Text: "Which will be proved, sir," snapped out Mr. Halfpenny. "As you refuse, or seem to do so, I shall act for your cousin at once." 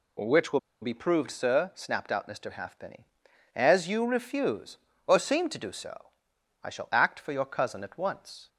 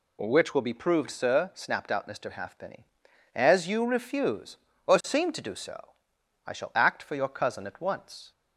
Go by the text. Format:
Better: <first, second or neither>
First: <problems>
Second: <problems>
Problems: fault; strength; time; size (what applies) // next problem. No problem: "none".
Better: second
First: pauses between "will" and "be"; slight; at 0.5 s; 0.23 s long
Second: none